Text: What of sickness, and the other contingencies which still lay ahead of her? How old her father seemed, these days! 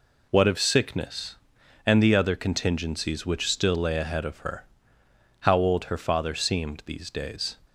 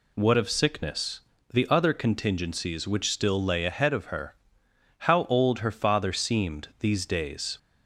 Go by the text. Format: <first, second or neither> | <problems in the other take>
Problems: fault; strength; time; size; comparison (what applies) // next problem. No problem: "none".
first | skips "and"; at 1.3 s